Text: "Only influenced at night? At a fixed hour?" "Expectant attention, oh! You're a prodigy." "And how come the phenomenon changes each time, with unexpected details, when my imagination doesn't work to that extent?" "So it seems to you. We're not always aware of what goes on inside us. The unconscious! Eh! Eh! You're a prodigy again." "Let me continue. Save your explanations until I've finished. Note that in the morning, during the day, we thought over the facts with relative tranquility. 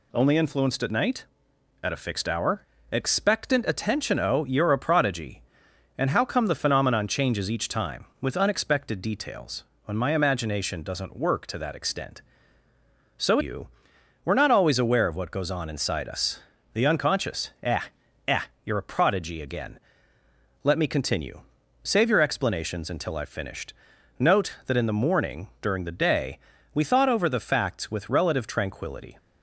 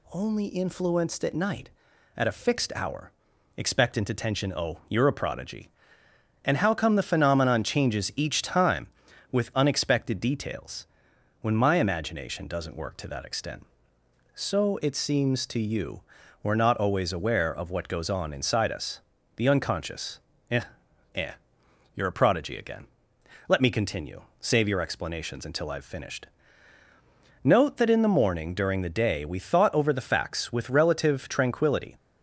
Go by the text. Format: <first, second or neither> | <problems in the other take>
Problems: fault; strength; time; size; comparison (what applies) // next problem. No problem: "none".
second | skips "it seems to"; at 13.3 s